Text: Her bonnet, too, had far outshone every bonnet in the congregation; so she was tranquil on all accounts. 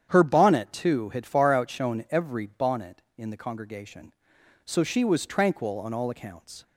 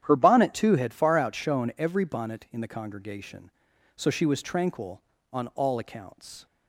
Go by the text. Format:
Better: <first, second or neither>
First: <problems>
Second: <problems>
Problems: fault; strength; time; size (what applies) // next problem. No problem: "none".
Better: neither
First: starts louder than the rest; strong; until 1.1 s; 9 dB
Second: starts louder than the rest; strong; until 1.0 s; 10 dB